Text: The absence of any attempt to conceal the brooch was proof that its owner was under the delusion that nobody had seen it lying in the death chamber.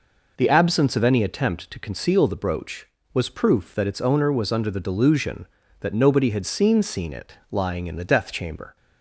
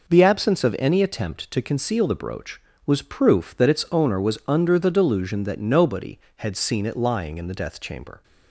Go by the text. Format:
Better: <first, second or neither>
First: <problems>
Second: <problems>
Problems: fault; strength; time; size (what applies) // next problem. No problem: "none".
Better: second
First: says "seen" twice; at 6.8 s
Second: none